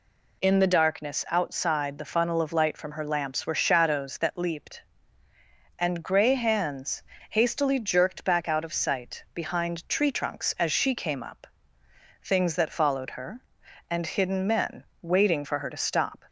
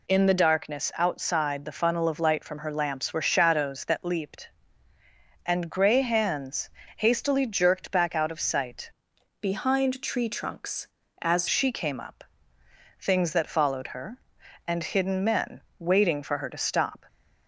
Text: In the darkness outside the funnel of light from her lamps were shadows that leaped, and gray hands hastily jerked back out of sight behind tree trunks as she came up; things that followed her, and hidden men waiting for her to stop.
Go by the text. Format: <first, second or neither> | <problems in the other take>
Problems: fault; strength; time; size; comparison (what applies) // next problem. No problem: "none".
first | pauses between "hands" and "hastily"; slight; at 6.6 s; 0.28 s long; slight in the first // changes voice from "behind" to "as"; from 9.4 to 11.4 s; 2.0 s long // pauses between "men" and "waiting"; slight; at 15.6 s; 0.18 s long; slight in the first